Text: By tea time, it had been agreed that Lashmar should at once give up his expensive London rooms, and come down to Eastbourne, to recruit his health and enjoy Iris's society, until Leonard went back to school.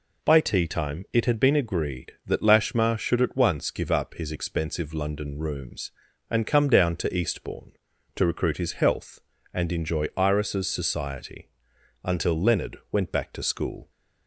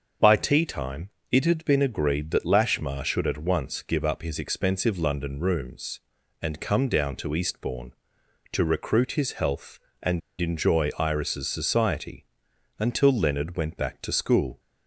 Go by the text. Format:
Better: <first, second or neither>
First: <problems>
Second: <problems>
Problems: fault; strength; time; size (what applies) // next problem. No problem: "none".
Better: first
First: none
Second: starts louder than the rest; until 1.4 s; 7 dB // pauses between "and" and "enjoy"; slight; at 10.2 s; 0.21 s long